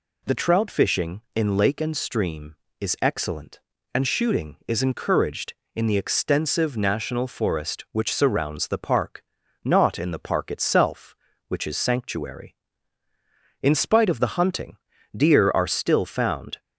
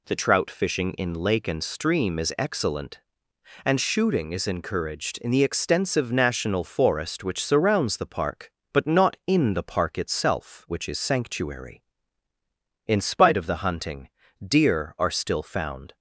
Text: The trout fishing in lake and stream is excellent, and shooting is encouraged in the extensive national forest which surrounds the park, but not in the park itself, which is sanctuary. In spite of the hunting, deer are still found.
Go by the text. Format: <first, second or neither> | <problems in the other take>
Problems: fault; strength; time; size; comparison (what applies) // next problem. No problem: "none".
second | skips "but"; at 9.4 s